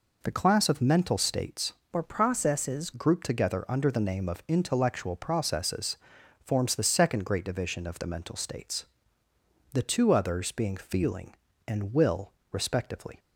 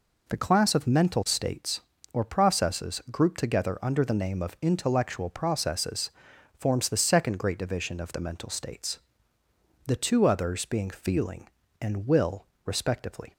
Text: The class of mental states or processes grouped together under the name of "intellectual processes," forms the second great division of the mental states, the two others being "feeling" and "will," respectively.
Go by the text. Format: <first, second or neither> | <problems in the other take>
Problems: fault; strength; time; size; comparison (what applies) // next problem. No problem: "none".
second | changes voice from "or" to "processes"; from 1.9 to 2.9 s; 1.0 s long